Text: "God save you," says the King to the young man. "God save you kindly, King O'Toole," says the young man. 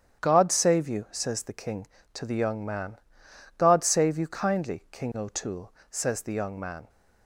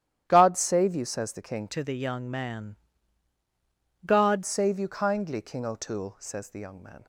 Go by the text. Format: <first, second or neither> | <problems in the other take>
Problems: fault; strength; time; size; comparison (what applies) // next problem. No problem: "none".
first | starts louder than the rest; strong; until 1.2 s; 11.5 dB; strong in the first // changes voice from "to" to "God"; from 1.6 to 4.4 s; 2.8 s long